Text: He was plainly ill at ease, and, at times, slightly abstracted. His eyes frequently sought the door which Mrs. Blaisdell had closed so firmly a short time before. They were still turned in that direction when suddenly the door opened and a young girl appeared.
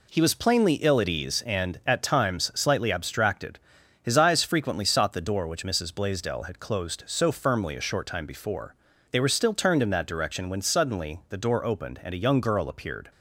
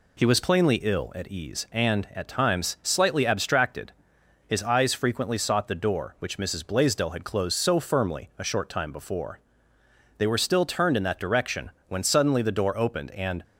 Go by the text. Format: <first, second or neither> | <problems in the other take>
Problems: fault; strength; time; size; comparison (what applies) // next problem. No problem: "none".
first | pauses between "direction" and "when"; slight; at 11.6 s; 0.18 s long // stops before "a young girl appeared"; at 13.4 s